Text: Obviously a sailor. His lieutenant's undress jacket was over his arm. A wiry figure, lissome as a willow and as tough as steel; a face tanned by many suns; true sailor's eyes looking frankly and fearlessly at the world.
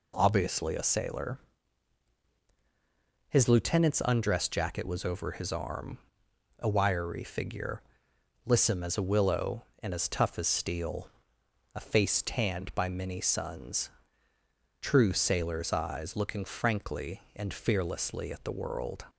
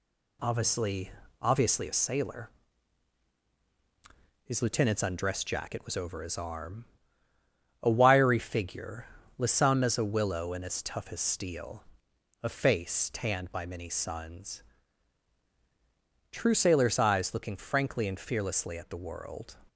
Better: first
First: none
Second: says "Obviously" twice; at 1.4 s

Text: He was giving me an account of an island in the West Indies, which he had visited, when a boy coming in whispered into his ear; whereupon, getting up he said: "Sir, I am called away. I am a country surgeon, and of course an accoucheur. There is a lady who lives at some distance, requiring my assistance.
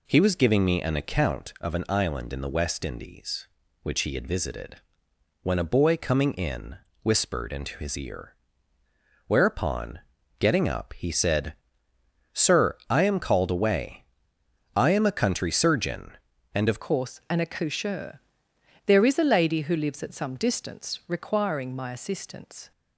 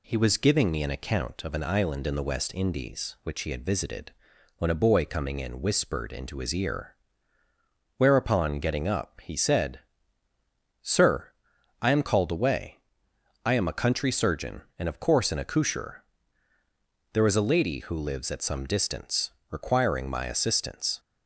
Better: second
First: pauses between "in" and "whispered"; slight; at 6.7 s; 0.26 s long // changes voice at "course"; from 16.8 s on; 5.9 s long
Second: none

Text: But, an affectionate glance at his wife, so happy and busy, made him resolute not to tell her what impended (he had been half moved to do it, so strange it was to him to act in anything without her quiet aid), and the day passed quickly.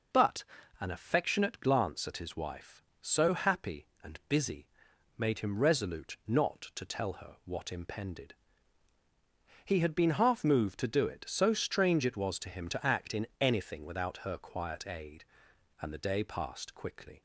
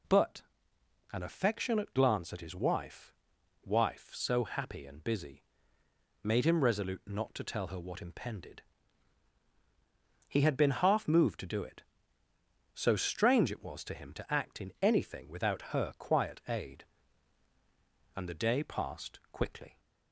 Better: first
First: none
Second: says "wife" twice; at 3.6 s

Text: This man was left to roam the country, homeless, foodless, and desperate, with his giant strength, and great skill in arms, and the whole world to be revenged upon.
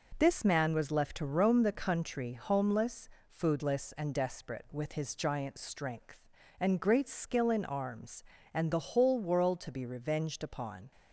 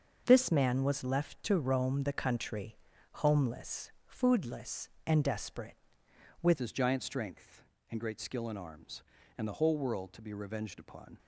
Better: first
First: none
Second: starts louder than the rest; until 1.2 s; 6.5 dB // changes voice at "his"; from 6.5 s on; 4.6 s long

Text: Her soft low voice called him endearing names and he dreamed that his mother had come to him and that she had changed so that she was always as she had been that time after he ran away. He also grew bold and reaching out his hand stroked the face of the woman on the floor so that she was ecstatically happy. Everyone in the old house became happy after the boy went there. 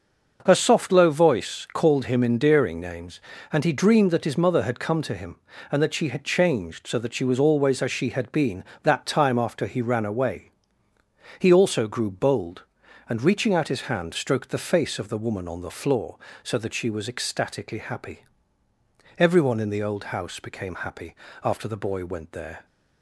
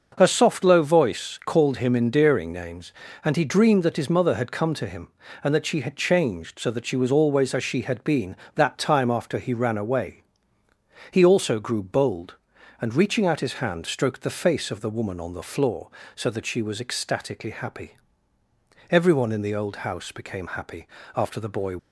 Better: first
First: pauses between "happy" and "after"; slight; at 21.1 s; 0.28 s long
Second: starts louder than the rest; noticeable; until 1.1 s; 6 dB // pauses between "happy" and "after"; slight; at 20.8 s; 0.28 s long // stops before "went there"; at 21.7 s

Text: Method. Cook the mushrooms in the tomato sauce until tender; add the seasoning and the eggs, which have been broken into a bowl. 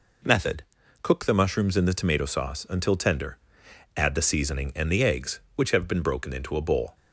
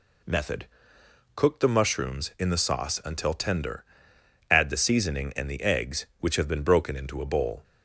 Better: first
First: none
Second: skips "tomato"; at 2.5 s

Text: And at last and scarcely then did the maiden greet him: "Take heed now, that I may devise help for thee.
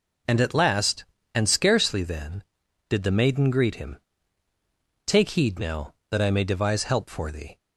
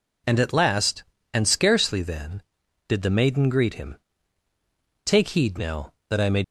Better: first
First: none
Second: stops before "devise help for thee"; at 6.4 s

